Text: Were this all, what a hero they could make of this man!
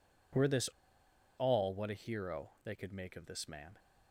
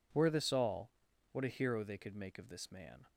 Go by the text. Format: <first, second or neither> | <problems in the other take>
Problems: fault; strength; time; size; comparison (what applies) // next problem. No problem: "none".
second | pauses between "this" and "all"; noticeable; at 0.6 s; 0.69 s long // pauses between "hero" and "they"; slight; at 2.4 s; 0.16 s long